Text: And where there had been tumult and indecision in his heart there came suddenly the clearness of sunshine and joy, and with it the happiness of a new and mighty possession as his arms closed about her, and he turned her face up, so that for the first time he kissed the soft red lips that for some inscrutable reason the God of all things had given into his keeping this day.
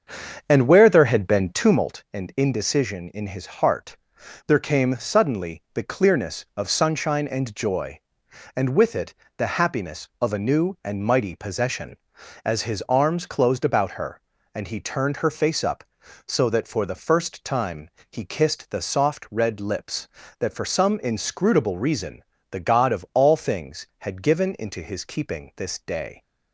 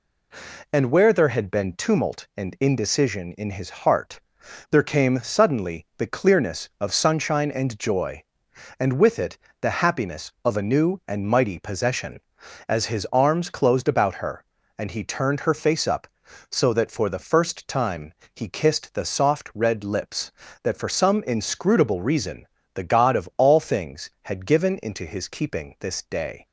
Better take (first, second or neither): second